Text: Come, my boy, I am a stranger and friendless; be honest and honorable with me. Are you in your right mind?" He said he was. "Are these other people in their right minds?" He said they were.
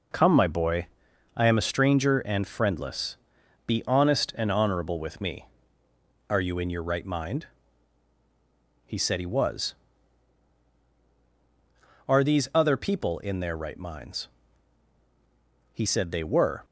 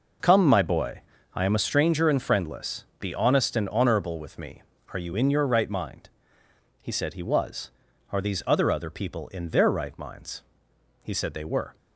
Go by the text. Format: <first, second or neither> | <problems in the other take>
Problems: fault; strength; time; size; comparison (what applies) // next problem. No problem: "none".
first | says "other" twice; at 8.6 s